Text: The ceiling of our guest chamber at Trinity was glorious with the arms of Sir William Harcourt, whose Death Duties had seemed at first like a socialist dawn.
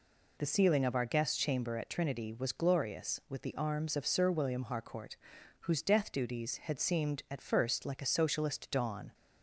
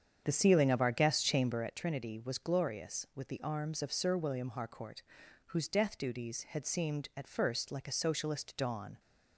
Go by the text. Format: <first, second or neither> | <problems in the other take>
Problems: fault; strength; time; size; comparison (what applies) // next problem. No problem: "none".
first | starts louder than the rest; strong; until 1.8 s; 8 dB